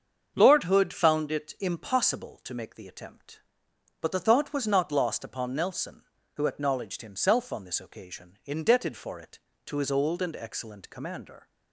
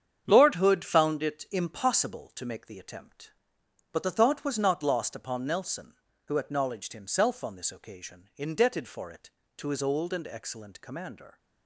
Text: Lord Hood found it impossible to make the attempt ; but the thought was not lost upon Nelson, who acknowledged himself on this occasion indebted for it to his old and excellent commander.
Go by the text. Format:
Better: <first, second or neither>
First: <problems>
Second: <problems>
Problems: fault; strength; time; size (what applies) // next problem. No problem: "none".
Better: first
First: starts louder than the rest; until 1.3 s; 7 dB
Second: gets quieter; strong; throughout; 8 dB // starts louder than the rest; strong; until 1.2 s; 8 dB